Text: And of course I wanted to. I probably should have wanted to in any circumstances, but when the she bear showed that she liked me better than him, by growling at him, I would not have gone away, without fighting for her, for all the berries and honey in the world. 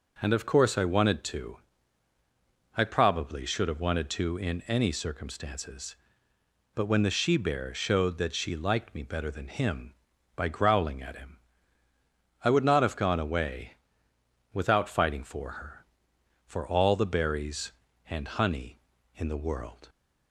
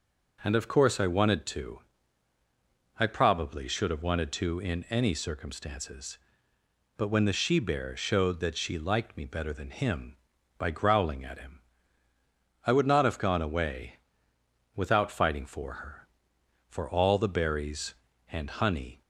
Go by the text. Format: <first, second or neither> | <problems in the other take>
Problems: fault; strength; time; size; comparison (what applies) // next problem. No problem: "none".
first | stops before "in the world"; at 19.0 s